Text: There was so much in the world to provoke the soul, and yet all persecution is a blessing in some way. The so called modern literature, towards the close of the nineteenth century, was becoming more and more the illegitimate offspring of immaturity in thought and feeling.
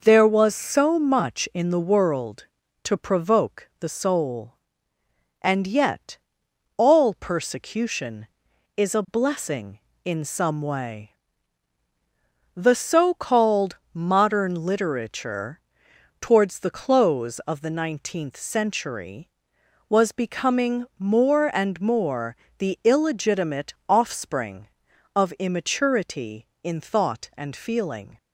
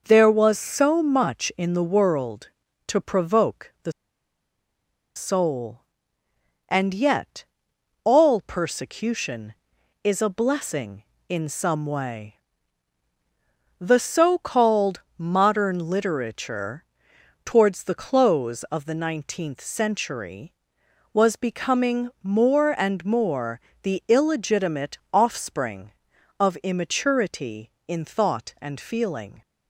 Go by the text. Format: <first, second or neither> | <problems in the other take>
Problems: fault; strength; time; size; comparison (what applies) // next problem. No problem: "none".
first | pauses between "the" and "soul"; at 3.9 s; 1.2 s long // pauses between "yet" and "all"; noticeable; at 7.4 s; 0.62 s long; noticeable in the first // pauses between "called" and "modern"; slight; at 15.0 s; 0.16 s long; slight in the first // pauses between "more" and "the"; slight; at 23.5 s; 0.24 s long; slight in the first